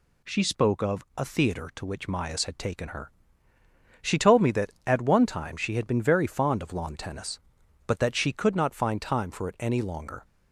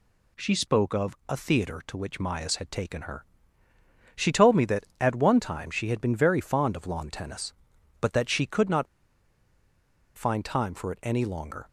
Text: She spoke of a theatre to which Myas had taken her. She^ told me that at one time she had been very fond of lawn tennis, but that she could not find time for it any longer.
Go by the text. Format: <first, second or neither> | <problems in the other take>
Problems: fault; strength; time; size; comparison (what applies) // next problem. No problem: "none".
first | pauses between "not" and "find"; strong; at 8.8 s; 1.3 s long